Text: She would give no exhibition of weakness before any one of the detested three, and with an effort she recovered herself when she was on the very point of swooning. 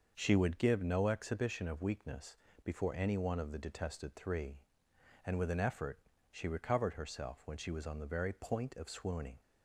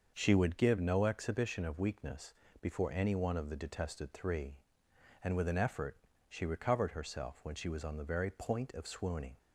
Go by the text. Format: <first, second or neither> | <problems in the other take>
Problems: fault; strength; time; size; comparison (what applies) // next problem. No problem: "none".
neither | starts louder than the rest; the same in both // pauses between "weakness" and "before"; slight; the same in both // pauses between "effort" and "she"; slight; the same in both